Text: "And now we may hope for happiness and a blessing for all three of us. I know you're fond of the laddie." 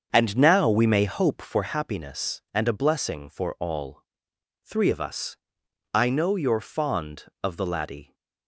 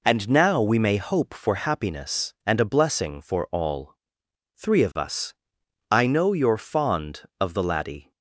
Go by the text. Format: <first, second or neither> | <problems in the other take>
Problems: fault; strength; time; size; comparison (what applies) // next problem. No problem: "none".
second | starts louder than the rest; until 1.7 s; 7 dB // pauses between "all" and "three"; noticeable; at 4.0 s; 0.62 s long; noticeable in the second